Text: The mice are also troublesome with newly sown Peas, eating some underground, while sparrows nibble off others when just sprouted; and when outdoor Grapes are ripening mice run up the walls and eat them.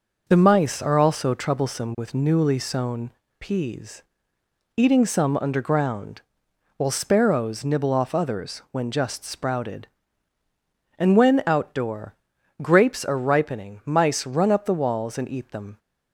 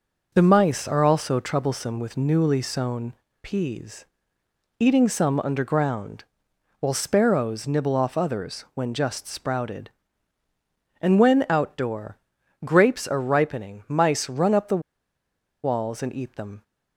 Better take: first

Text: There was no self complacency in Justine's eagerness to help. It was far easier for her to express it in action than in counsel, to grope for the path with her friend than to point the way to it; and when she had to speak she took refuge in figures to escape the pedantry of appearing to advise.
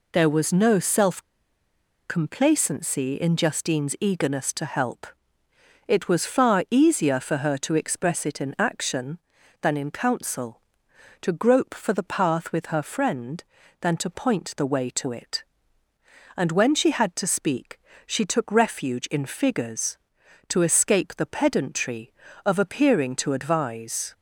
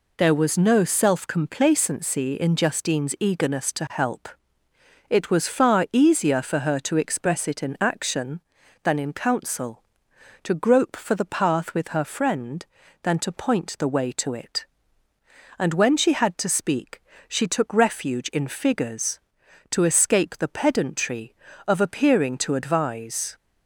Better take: second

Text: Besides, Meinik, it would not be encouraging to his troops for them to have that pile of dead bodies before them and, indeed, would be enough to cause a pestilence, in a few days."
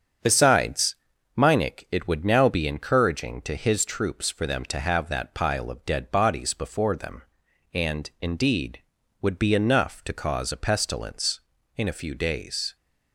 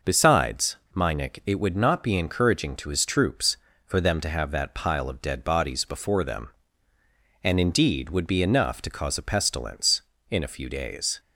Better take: second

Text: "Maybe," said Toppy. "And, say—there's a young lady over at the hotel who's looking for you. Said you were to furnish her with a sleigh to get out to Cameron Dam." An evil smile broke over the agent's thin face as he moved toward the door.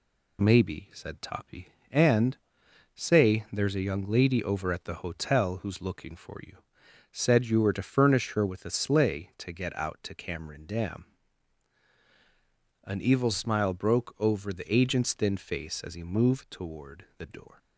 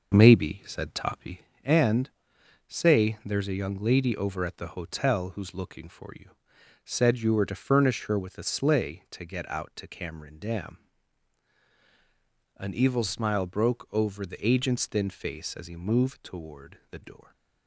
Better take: first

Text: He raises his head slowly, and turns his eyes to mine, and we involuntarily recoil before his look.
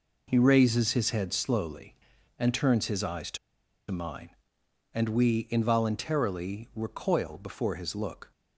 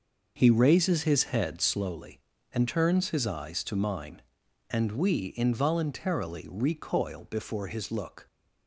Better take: second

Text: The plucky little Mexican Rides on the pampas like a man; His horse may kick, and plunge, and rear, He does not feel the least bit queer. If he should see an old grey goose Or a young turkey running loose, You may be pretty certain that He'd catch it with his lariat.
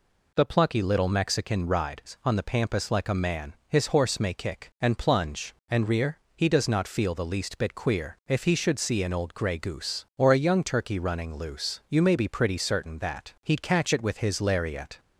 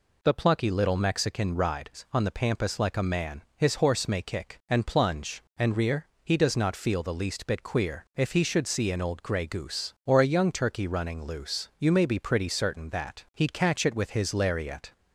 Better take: neither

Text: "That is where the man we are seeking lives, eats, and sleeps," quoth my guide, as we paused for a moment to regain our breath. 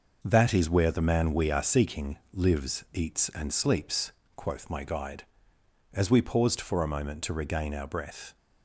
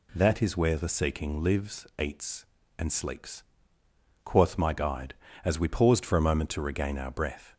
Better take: first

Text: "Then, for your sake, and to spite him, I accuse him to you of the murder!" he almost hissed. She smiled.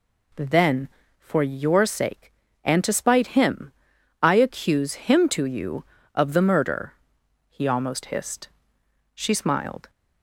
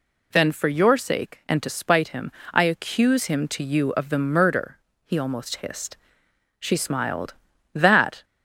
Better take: first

